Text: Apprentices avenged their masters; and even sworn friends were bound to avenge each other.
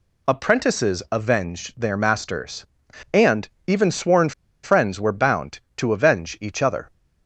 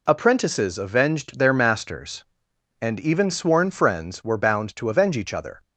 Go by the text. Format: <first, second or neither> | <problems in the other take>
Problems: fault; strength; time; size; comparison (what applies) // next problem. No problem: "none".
second | pauses between "and" and "even"; slight; at 3.4 s; 0.20 s long // pauses between "sworn" and "friends"; slight; at 4.3 s; 0.32 s long